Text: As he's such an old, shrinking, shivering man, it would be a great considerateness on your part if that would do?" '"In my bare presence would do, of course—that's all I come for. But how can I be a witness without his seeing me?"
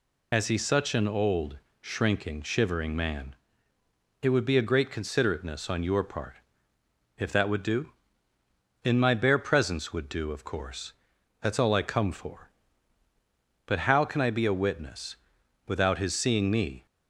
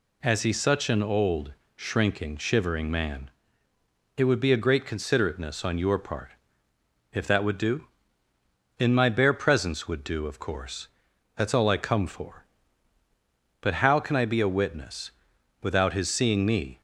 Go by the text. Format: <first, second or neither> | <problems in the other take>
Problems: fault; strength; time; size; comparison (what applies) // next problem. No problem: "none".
second | loses the start of "As"; at 0.3 s; 45 ms // pauses between "part" and "if"; noticeable; at 6.3 s; 0.82 s long; noticeable in the second // pauses between "witness" and "without"; noticeable; at 15.1 s; 0.52 s long; noticeable in the second